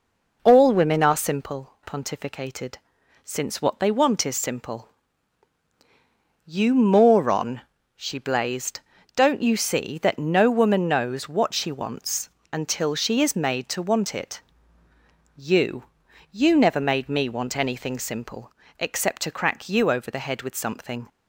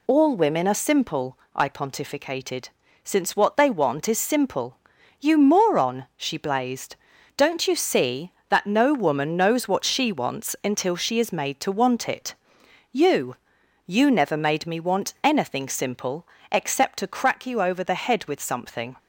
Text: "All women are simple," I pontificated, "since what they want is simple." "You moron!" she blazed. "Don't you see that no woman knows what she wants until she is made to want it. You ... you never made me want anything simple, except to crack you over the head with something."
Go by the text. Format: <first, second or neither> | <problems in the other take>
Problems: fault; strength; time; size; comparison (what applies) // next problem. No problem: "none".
second | skips "I"; at 1.7 s // pauses between "wants" and "until"; slight; at 12.3 s; 0.22 s long